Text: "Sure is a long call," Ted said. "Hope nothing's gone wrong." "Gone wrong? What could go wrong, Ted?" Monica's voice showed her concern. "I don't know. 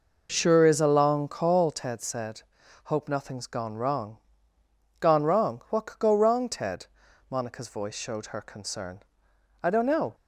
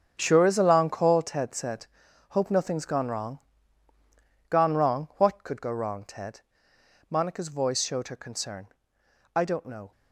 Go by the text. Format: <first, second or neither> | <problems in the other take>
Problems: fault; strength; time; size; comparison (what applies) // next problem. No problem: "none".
first | gets quieter; strong; throughout; 12.5 dB